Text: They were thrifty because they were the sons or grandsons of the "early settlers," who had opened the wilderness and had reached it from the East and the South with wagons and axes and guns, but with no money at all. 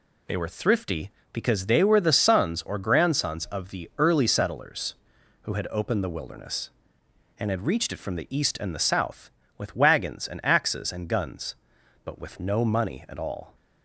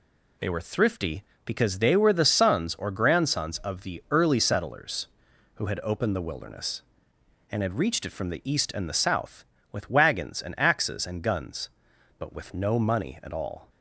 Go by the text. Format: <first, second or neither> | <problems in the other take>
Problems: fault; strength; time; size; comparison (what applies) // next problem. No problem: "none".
neither | none